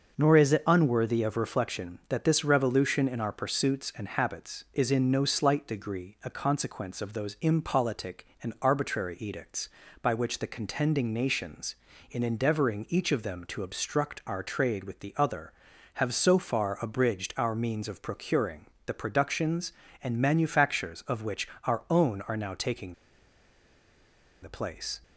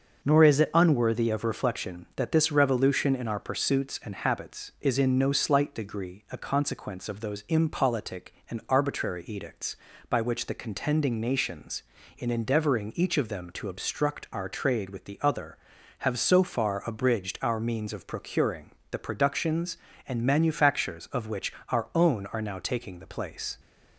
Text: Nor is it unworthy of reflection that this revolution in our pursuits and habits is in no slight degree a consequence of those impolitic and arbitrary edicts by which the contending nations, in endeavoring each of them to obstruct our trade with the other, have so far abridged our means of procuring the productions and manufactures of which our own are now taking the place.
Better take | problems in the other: second | starts louder than the rest; noticeable; until 1.1 s; 6 dB; noticeable in the second // pauses between "procuring" and "the"; slight; at 18.6 s; 0.18 s long; slight in the second // pauses between "which" and "our"; slight; at 21.4 s; 0.18 s long; slight in the second // pauses between "taking" and "the"; strong; at 22.9 s; 1.4 s long

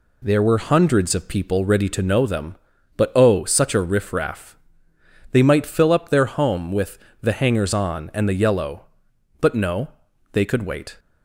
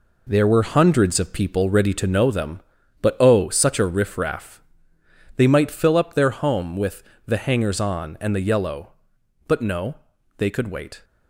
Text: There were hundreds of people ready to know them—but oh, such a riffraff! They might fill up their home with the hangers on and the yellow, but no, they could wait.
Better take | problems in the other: first | gets quieter; strong; throughout; 8 dB // pauses between "with" and "the"; slight; at 7.0 s; 0.22 s long; slight in the first

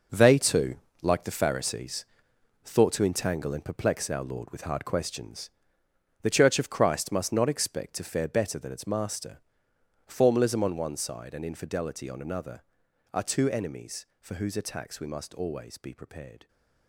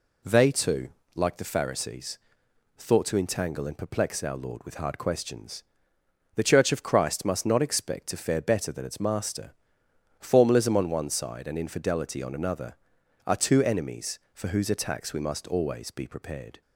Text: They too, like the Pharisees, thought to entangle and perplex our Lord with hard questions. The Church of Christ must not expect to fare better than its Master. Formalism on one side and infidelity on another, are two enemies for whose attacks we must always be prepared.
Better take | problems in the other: second | gets quieter; strong; throughout; 12 dB

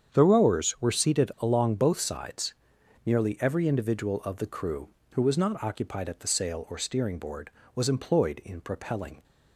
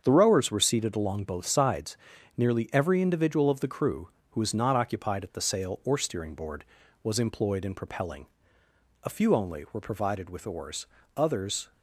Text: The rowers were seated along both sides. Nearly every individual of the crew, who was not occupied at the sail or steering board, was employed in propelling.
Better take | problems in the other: first | starts louder than the rest; strong; until 1.0 s; 7 dB; strong in the first // goes on to say "A few only were provided with oars others"; strong; from 9.0 s on; 2.6 s long

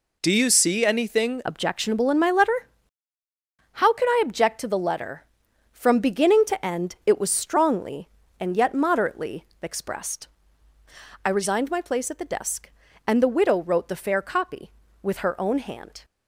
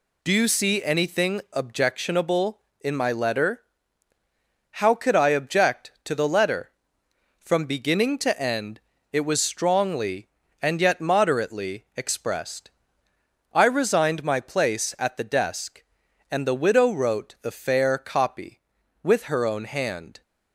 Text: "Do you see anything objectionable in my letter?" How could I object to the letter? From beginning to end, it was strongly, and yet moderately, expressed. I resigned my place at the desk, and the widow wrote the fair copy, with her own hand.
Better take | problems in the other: second | changes voice at "objectionable"; from 1.4 s on; 14.6 s long

